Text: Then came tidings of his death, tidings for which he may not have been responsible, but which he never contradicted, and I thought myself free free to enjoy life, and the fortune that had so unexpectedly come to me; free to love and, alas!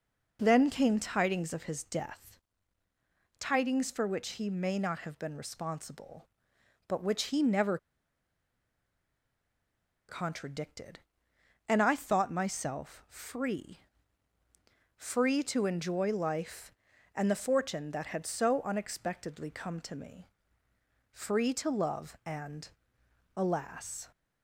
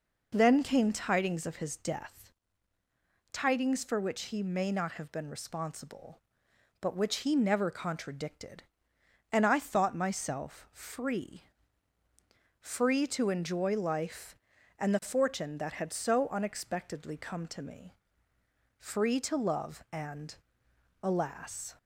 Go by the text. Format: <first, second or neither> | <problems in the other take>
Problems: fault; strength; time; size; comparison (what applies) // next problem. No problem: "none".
second | pauses between "never" and "contradicted"; strong; at 7.7 s; 2.3 s long // pauses between "free" and "free"; at 13.7 s; 1.1 s long; also in the second